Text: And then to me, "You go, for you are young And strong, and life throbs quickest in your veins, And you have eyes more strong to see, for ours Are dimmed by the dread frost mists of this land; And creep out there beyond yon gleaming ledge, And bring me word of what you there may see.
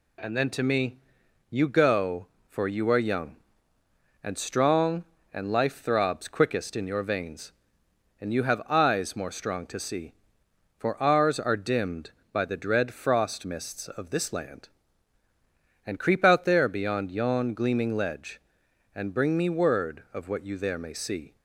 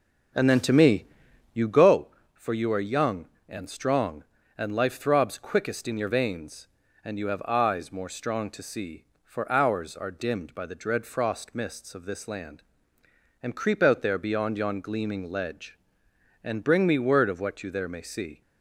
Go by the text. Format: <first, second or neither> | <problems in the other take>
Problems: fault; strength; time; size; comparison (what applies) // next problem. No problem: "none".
first | starts louder than the rest; noticeable; until 1.9 s; 5.5 dB